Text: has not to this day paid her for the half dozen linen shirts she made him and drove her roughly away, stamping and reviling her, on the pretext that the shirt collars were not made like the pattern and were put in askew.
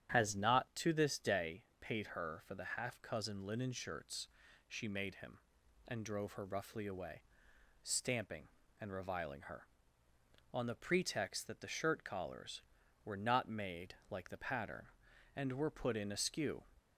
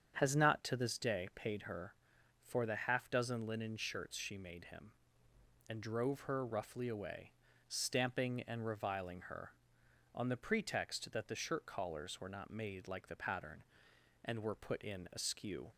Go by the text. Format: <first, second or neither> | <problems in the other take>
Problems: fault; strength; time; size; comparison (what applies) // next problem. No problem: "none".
second | starts louder than the rest; strong; until 1.1 s; 9 dB; strong in the second // pauses between "day" and "paid"; slight; at 1.6 s; 0.18 s long // says "cousin" for "dozen"; at 3.0 s // pauses between "shirts" and "she"; at 4.2 s; 0.40 s long // pauses between "made" and "like"; slight; at 13.9 s; 0.16 s long